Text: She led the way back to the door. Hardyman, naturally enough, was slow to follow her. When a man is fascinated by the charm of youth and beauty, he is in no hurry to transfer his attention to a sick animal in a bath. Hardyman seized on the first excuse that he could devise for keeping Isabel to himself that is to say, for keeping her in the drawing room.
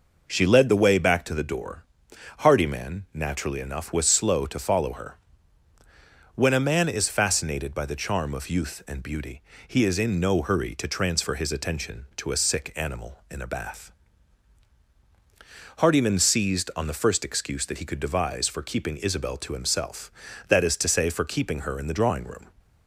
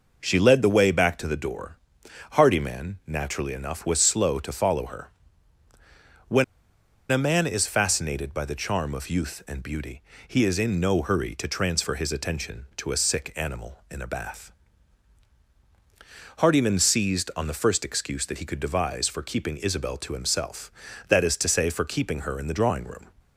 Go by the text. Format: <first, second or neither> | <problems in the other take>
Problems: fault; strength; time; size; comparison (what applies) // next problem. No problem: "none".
first | pauses between "When" and "a"; noticeable; at 6.4 s; 0.67 s long